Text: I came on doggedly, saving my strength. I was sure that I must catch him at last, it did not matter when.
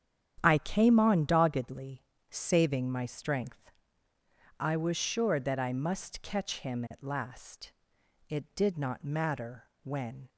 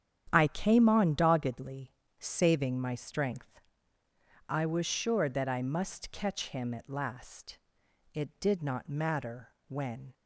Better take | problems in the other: neither | starts louder than the rest; strong; the same in both // pauses between "matter" and "when"; slight; the same in both

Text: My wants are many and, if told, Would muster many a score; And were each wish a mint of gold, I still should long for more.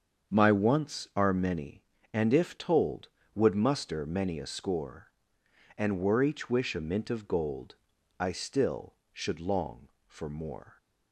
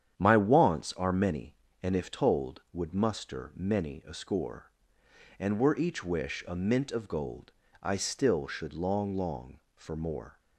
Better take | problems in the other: first | starts louder than the rest; strong; until 1.1 s; 9 dB; strong in the first // says "long" twice; at 9.1 s

